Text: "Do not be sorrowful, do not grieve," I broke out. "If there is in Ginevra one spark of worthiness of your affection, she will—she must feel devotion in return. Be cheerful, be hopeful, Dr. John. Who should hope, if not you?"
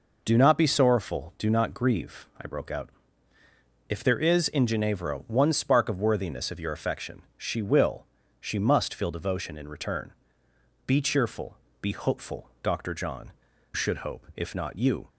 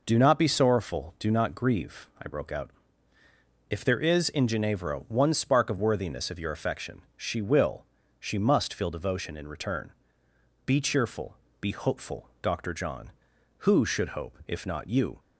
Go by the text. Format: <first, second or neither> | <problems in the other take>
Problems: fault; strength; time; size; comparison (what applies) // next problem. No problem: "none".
second | skips "Who"; at 13.5 s